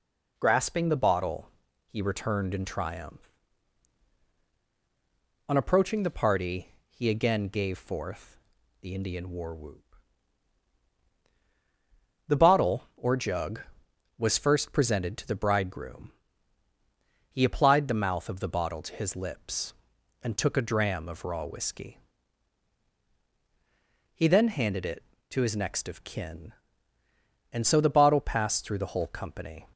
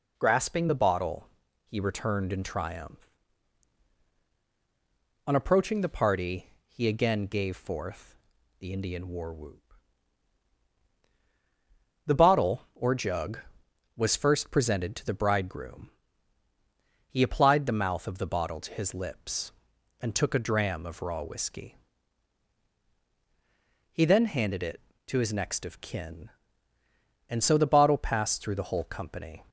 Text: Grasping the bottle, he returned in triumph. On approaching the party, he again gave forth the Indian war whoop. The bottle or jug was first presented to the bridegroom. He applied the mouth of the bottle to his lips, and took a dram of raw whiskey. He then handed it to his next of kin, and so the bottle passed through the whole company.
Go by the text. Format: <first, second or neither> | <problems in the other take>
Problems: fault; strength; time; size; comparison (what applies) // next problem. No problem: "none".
neither | pauses between "forth" and "the"; the same in both